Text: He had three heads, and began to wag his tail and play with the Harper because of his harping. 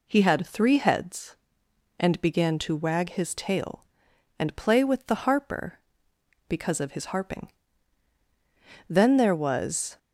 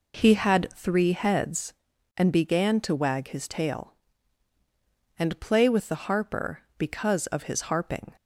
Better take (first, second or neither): second